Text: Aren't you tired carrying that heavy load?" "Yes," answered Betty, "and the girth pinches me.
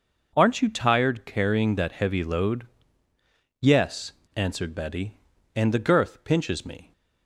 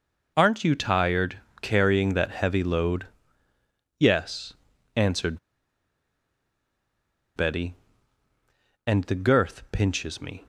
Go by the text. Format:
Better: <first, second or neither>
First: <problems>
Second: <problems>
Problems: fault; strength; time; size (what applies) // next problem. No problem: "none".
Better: first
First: none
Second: pauses between "tired" and "carrying"; slight; at 1.3 s; 0.20 s long // pauses between "answered" and "Betty"; strong; at 5.3 s; 1.9 s long